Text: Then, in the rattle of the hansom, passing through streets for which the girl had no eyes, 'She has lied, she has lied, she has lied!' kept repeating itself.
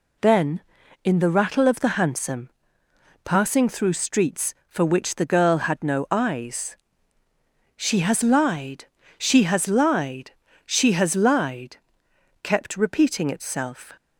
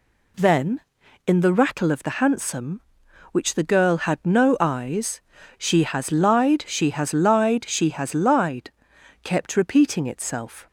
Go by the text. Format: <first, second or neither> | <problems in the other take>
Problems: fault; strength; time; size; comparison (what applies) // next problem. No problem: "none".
first | skips "passing through streets for"; at 3.0 s